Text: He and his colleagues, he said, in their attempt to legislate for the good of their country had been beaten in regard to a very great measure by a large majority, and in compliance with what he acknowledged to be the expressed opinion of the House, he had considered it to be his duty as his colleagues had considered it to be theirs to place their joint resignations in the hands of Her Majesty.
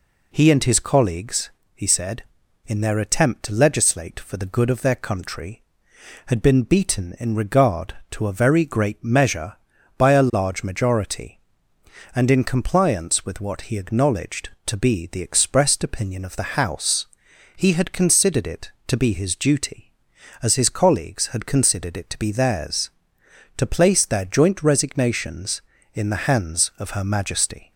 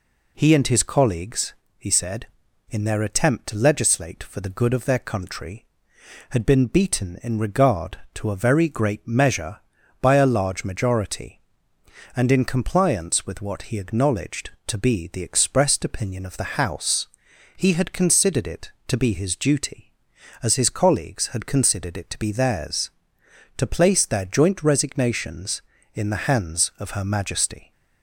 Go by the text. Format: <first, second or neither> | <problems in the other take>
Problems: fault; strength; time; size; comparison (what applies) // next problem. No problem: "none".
neither | none